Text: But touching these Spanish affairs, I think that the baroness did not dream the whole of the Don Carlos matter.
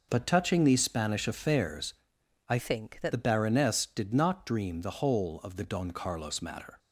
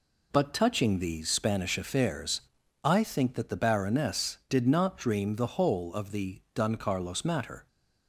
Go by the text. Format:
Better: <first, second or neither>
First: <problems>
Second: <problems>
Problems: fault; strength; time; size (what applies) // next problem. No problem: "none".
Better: second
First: changes voice from "think" to "that"; from 2.5 to 3.1 s; 0.6 s long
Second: none